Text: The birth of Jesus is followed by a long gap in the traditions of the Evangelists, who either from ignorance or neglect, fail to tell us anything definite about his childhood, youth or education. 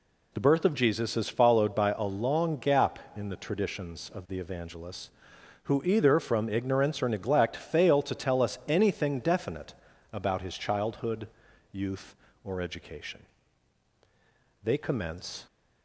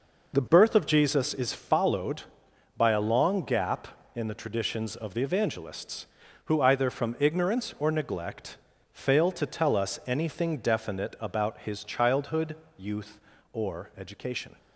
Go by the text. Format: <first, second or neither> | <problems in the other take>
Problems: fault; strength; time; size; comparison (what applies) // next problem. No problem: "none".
second | pauses between "definite" and "about"; at 9.7 s; 0.38 s long // goes on to say "They commence"; noticeable; from 14.6 s on; 0.82 s long